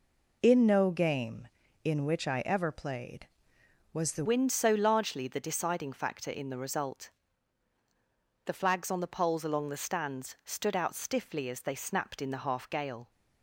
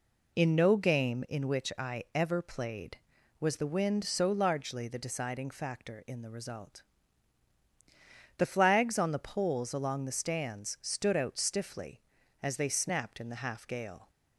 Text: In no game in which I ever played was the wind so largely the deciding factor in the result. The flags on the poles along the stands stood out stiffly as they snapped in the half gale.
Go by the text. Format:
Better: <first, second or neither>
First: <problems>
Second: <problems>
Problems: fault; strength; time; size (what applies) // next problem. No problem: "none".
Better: second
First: changes voice at "wind"; from 4.2 s on; 8.9 s long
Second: none